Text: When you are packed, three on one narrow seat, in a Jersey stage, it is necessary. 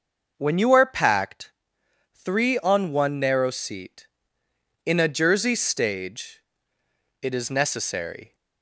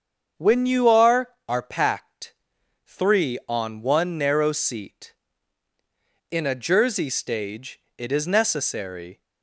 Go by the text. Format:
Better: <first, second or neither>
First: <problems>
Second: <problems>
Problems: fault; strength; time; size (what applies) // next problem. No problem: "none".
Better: first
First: starts louder than the rest; noticeable; until 1.3 s; 6 dB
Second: starts louder than the rest; strong; until 1.5 s; 7 dB // says "are" twice; at 1.4 s